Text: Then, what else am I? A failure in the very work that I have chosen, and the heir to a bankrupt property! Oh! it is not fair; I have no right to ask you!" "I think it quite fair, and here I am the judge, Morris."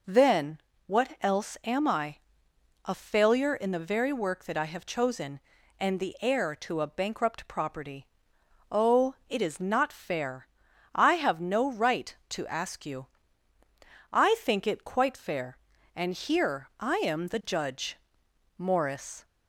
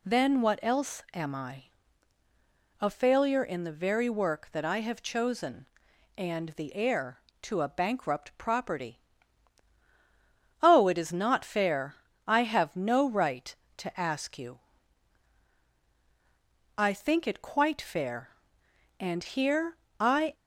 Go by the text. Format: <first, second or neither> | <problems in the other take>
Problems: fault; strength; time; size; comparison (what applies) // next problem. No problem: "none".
first | pauses between "here" and "I"; slight; at 19.7 s; 0.24 s long // stops before "am the judge Morris"; at 20.3 s